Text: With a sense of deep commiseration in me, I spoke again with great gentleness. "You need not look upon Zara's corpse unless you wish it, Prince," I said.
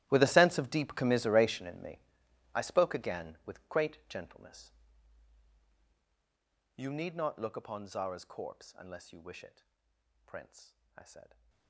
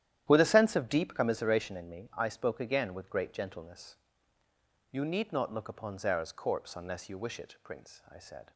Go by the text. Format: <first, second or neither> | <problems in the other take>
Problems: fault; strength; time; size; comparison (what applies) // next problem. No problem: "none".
second | gets quieter; strong; throughout; 18.5 dB // starts louder than the rest; strong; until 1.1 s; 13.5 dB; strong in the second